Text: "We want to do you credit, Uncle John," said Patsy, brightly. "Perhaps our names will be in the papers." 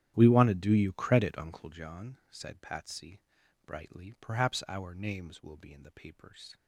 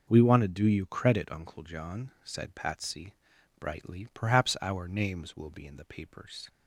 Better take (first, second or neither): second